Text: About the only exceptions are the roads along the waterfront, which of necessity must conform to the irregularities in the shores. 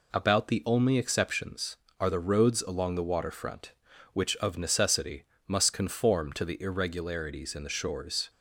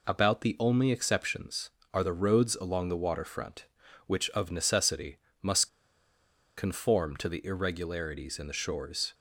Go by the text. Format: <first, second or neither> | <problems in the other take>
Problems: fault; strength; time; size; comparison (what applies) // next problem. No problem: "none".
first | pauses between "necessity" and "must"; slight; at 5.1 s; 0.24 s long; slight in the first // pauses between "must" and "conform"; noticeable; at 5.6 s; 0.87 s long